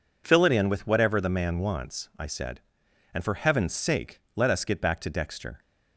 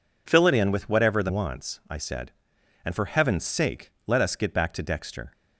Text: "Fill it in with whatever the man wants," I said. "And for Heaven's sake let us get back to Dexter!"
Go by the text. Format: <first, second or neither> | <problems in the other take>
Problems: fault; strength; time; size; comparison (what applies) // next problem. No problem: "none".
first | skips "man"; at 1.2 s